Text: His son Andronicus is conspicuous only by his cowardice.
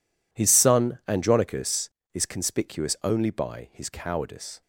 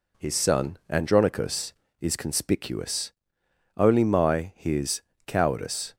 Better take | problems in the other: first | pauses between "conspicuous" and "only"; noticeable; at 3.1 s; 0.66 s long // says "my" for "by"; at 4.0 s // pauses between "his" and "cowardice"; slight; at 5.0 s; 0.26 s long

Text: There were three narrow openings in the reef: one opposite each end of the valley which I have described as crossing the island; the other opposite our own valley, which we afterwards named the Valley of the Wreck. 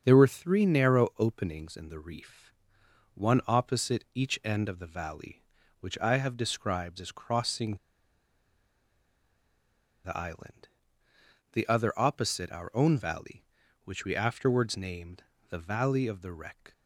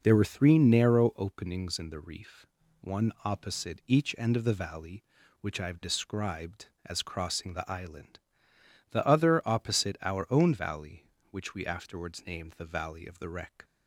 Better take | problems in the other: second | starts louder than the rest; until 1.0 s; 7 dB // pauses between "crossing" and "the"; strong; at 7.7 s; 2.2 s long // pauses between "named" and "the"; slight; at 15.2 s; 0.28 s long

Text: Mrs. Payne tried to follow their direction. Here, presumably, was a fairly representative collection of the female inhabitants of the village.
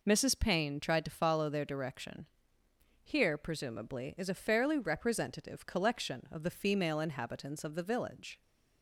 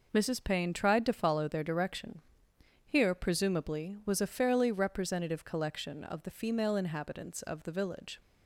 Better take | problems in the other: second | says "is" for "was"; at 4.1 s

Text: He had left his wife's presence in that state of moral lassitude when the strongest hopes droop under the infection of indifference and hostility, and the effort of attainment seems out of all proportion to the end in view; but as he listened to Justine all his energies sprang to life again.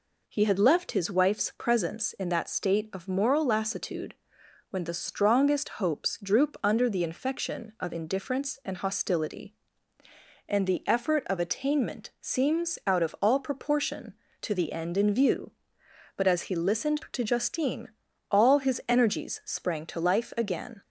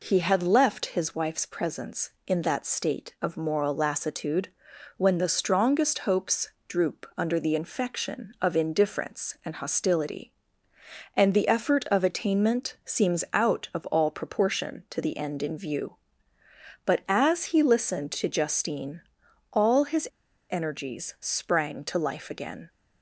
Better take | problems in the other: first | pauses between "lassitude" and "when"; noticeable; at 4.4 s; 0.48 s long; noticeable in the first // pauses between "hopes" and "droop"; slight; at 6.4 s; 0.18 s long // pauses between "Justine" and "all"; noticeable; at 19.0 s; 0.50 s long; also in the first // pauses between "his" and "energies"; at 20.0 s; 0.42 s long

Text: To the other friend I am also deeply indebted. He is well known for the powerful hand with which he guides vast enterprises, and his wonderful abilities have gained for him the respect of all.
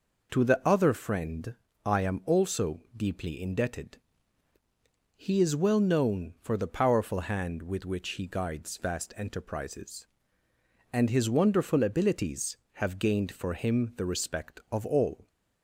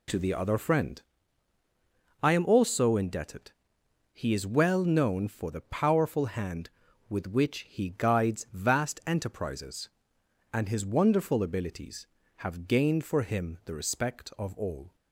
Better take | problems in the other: first | pauses between "friend" and "I"; at 0.9 s; 1.2 s long; slight in the first // skips "deeply"; at 2.9 s

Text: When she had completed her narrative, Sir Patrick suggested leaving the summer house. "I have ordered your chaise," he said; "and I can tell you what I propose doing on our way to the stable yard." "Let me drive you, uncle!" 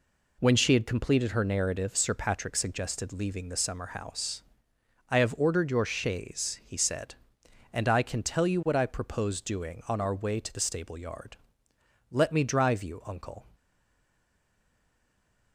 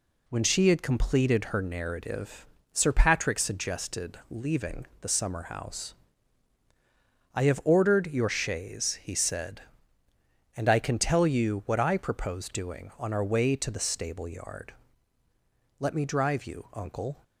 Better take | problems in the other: second | stays silent after the last word; noticeable; from 13.5 s on; 2.0 s long

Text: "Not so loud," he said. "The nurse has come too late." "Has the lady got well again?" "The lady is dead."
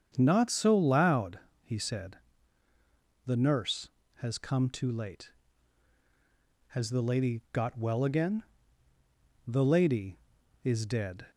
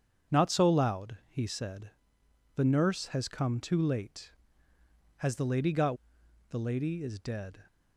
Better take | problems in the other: first | starts louder than the rest; strong; until 1.4 s; 7.5 dB; strong in the first // skips "well again"; at 6.2 s

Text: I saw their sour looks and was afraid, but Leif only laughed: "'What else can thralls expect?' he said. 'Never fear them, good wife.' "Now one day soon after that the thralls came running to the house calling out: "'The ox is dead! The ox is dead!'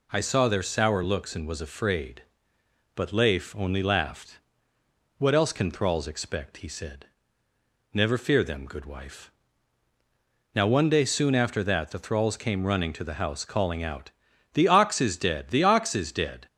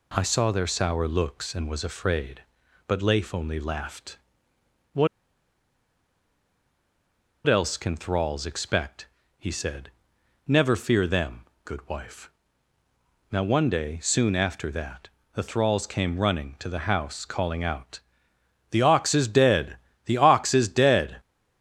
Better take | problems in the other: first | pauses between "What" and "else"; strong; at 5.0 s; 2.3 s long // pauses between "that" and "the"; slight; at 15.0 s; 0.26 s long

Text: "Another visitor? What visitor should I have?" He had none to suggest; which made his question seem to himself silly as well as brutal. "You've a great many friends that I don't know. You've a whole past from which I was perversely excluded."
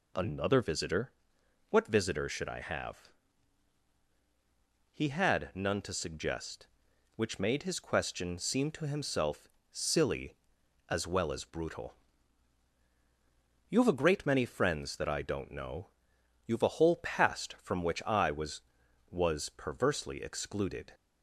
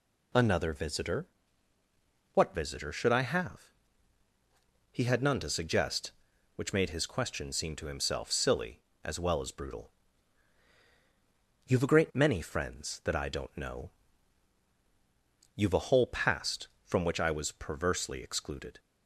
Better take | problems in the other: second | pauses between "himself" and "silly"; slight; at 9.4 s; 0.24 s long // says "was" twice; at 19.0 s

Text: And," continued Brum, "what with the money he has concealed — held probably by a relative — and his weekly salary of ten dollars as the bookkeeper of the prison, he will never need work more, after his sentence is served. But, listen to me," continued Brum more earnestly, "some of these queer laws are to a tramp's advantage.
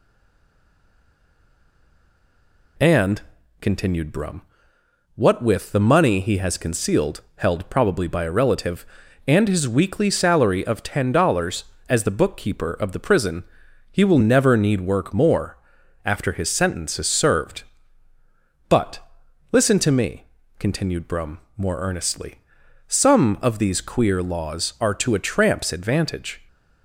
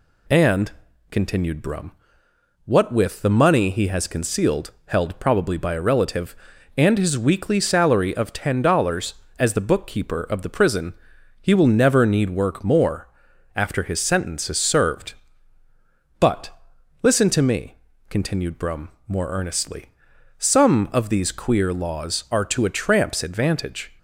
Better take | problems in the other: second | stays silent before the first word; strong; until 2.7 s; 2.7 s long // pauses between "Brum" and "more"; slight; at 21.3 s; 0.18 s long; slight in the second

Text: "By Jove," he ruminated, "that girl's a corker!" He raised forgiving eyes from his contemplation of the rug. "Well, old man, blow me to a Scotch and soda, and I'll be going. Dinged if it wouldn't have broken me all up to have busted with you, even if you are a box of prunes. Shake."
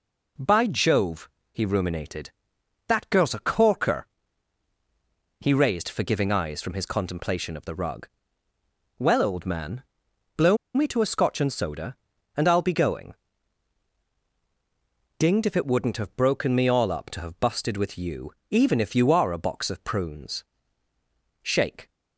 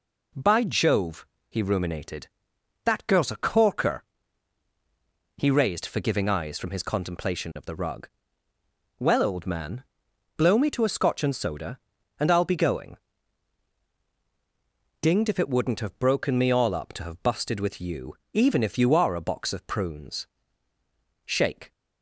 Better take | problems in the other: second | pauses between "blow" and "me"; slight; at 10.5 s; 0.18 s long

